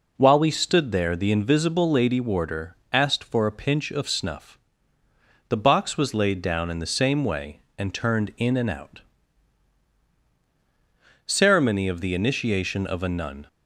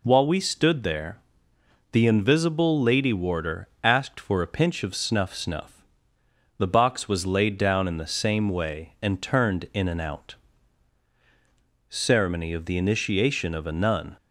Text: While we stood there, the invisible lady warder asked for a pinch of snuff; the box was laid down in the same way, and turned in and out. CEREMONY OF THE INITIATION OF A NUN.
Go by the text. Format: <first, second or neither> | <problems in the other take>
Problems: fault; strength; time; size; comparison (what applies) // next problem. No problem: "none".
first | pauses between "warder" and "asked"; slight; at 3.6 s; 0.16 s long; slight in the first // says "snuff" twice; at 5.3 s